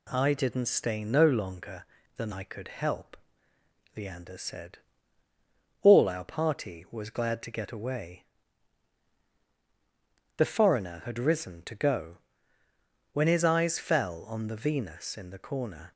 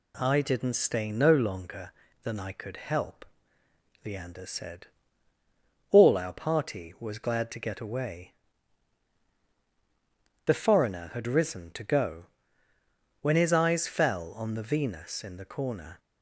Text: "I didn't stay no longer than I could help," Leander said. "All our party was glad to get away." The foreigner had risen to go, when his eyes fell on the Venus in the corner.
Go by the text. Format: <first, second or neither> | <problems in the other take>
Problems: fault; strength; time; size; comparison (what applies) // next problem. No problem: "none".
neither | none